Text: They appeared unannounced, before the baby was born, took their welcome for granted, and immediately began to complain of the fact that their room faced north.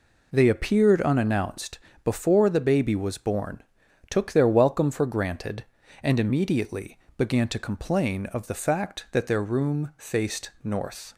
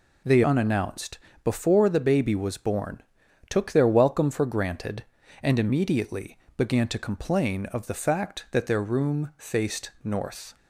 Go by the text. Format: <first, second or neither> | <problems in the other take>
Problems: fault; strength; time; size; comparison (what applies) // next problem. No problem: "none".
first | skips "appeared"; at 0.4 s // pauses between "immediately" and "began"; slight; at 6.3 s; 0.18 s long; slight in the first